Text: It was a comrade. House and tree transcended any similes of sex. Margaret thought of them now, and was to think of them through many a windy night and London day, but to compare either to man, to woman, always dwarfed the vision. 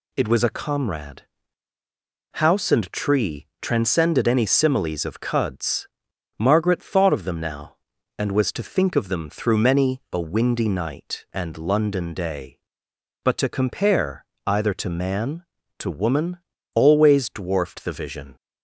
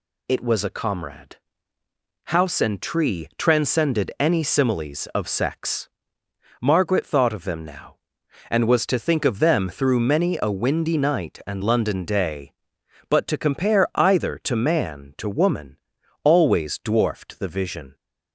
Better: second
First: pauses between "tree" and "transcended"; slight; at 3.4 s; 0.16 s long // says "cuds" for "sex"; at 5.2 s // pauses between "compare" and "either"; slight; at 14.2 s; 0.20 s long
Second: none

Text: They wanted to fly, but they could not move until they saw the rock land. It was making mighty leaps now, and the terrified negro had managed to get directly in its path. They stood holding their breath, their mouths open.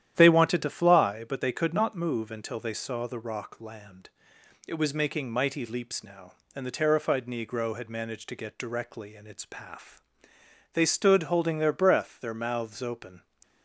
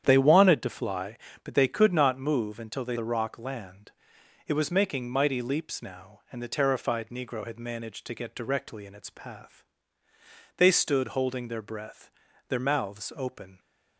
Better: first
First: starts louder than the rest; strong; until 1.1 s; 10.5 dB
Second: starts louder than the rest; strong; until 1.0 s; 9 dB // skips "saw"; at 2.9 s

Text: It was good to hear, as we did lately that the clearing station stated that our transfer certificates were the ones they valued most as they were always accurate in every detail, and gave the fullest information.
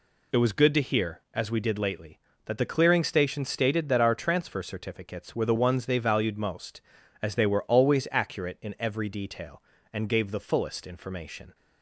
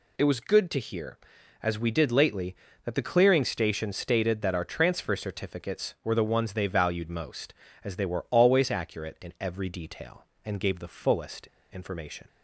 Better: first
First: none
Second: pauses between "fullest" and "information"; slight; at 11.4 s; 0.22 s long

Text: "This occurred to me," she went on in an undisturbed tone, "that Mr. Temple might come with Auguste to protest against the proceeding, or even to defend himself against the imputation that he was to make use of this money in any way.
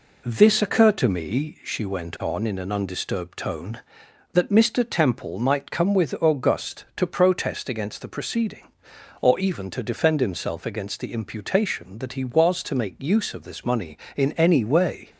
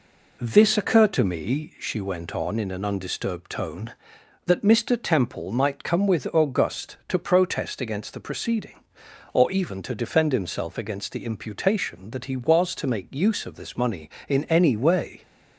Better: neither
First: none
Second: none

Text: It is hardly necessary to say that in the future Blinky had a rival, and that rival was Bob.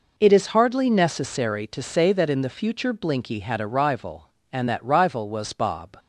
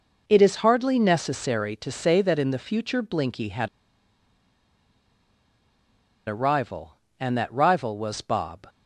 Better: first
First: none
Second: pauses between "had" and "a"; strong; at 3.6 s; 2.5 s long

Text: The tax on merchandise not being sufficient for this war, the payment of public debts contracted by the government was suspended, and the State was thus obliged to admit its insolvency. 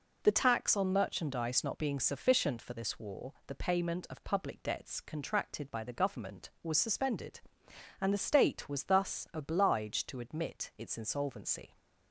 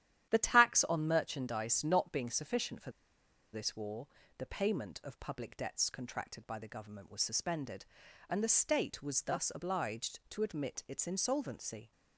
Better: first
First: none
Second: starts louder than the rest; strong; until 1.3 s; 11 dB // pauses between "for" and "this"; noticeable; at 2.9 s; 0.62 s long

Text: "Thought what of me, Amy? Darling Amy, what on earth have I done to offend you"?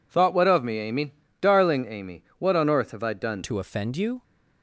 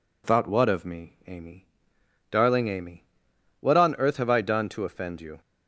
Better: second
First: changes voice at "to"; from 3.4 s on; 0.8 s long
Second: none

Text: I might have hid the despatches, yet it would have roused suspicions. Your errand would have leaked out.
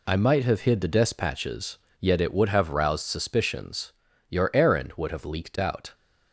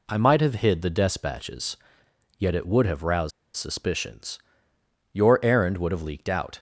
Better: first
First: none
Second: pauses between "roused" and "suspicions"; slight; at 3.3 s; 0.25 s long

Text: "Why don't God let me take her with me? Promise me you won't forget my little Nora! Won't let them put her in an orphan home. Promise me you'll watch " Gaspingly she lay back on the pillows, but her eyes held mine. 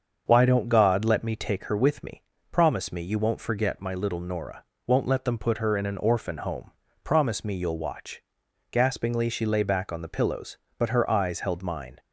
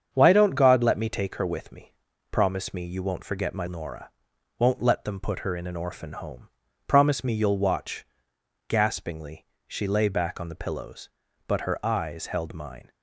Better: first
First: starts louder than the rest; until 1.2 s; 7 dB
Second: starts louder than the rest; strong; until 1.1 s; 8 dB // skips "little"; at 3.6 s // pauses between "Gaspingly" and "she"; slight; at 9.4 s; 0.20 s long

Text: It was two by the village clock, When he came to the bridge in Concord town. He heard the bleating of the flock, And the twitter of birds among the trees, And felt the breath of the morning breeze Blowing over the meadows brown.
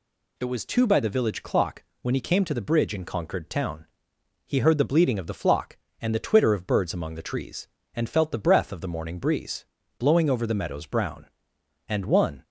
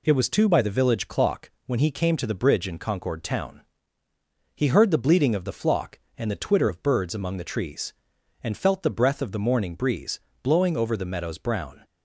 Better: second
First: pauses between "breeze" and "Blowing"; slight; at 9.6 s; 0.34 s long // goes on to say "And one"; from 11.8 s on; 0.56 s long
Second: pauses between "breeze" and "Blowing"; slight; at 10.1 s; 0.24 s long

